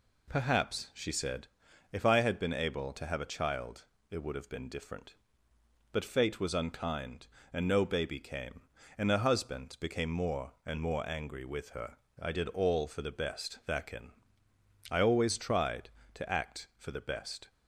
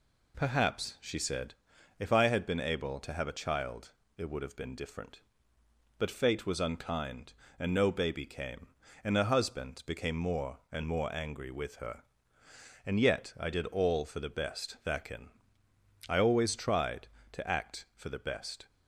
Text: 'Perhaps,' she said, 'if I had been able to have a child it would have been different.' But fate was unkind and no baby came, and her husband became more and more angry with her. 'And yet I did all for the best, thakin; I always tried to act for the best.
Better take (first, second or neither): second